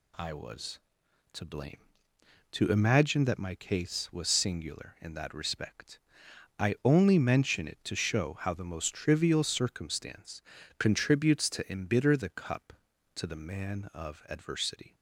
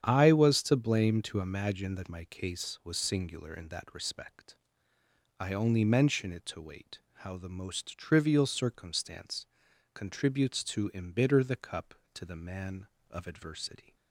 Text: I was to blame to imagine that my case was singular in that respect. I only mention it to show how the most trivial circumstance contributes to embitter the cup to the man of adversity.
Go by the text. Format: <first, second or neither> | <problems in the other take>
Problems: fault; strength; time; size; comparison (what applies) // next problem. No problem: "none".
first | starts louder than the rest; strong; until 1.0 s; 9 dB // says "wait" for "show"; at 6.6 s // pauses between "circumstance" and "contributes"; noticeable; at 9.4 s; 0.50 s long; also in the first